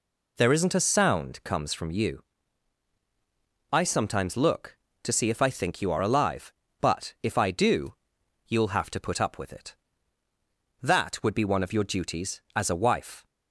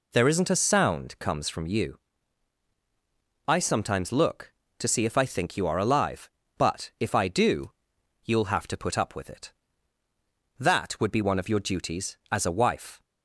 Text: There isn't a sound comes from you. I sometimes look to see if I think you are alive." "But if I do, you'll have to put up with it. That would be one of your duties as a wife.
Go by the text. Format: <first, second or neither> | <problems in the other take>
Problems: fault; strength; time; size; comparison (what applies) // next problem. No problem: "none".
neither | none